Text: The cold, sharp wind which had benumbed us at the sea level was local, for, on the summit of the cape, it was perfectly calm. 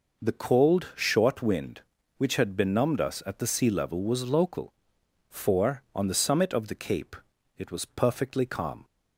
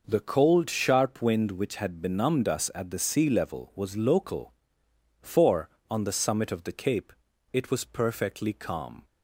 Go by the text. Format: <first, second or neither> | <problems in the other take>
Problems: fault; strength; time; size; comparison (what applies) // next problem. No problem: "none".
second | says "short" for "sharp"; at 0.9 s